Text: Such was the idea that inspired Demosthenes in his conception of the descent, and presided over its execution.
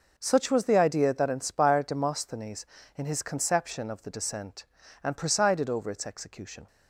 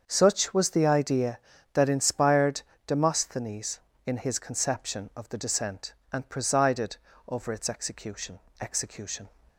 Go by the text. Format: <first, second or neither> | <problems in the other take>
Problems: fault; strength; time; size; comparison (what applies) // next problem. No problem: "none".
first | starts louder than the rest; until 1.0 s; 7 dB // pauses between "inspired" and "Demosthenes"; slight; at 2.6 s; 0.24 s long // pauses between "presided" and "over"; slight; at 6.9 s; 0.30 s long // says "execution" twice; at 8.6 s